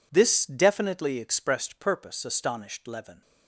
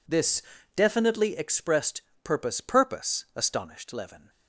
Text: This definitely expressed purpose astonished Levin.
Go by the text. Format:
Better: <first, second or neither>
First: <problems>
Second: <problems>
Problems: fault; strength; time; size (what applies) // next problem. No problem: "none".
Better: first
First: none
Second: pauses between "This" and "definitely"; slight; at 0.4 s; 0.34 s long // pauses between "expressed" and "purpose"; slight; at 2.0 s; 0.22 s long // says "purpose" twice; at 2.5 s